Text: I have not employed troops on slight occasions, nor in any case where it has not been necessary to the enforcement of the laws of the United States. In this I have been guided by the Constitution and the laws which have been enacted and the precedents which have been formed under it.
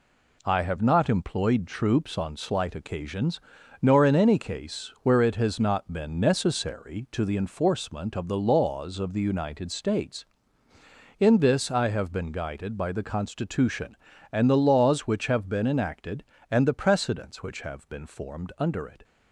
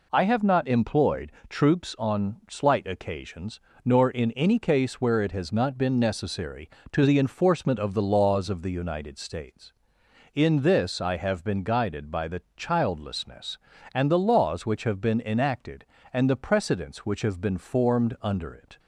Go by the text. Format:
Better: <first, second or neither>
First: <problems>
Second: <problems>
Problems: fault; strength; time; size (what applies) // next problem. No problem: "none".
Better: first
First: none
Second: pauses between "employed" and "troops"; slight; at 1.3 s; 0.18 s long // says "Childlessness" for "Constitution"; at 12.5 s